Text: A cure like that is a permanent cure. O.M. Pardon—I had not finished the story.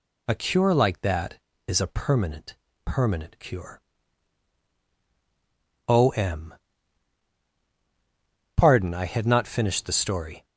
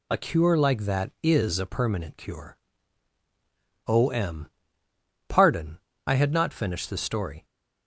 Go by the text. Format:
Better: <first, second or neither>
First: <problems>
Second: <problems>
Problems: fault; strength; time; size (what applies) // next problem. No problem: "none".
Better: second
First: says "permanent" twice; at 2.8 s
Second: none